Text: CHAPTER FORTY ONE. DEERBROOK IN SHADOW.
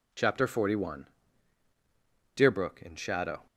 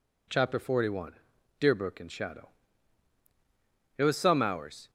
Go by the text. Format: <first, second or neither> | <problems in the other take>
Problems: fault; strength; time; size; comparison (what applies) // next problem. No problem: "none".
first | goes on to say "It was some hours"; noticeable; from 3.9 s on; 0.94 s long